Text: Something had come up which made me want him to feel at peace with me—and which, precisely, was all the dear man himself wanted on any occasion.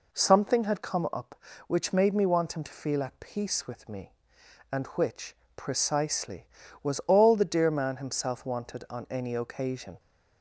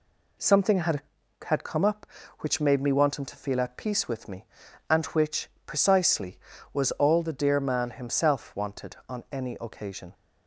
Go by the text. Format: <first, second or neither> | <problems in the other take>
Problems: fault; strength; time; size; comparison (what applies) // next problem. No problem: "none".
first | says "had" twice; at 1.4 s